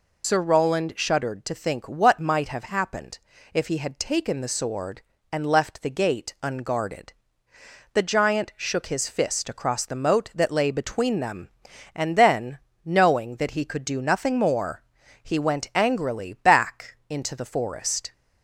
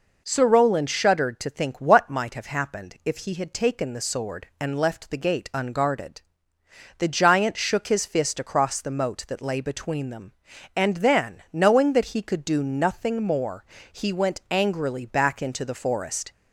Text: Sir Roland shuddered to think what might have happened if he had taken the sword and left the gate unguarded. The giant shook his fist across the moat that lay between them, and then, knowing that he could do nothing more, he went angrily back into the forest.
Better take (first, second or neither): second